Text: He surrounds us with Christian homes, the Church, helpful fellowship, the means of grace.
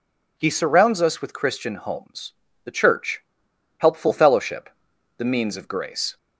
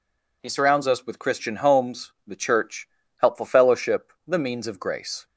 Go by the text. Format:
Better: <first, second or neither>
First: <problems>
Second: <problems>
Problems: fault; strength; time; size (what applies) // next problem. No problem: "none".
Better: neither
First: none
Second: none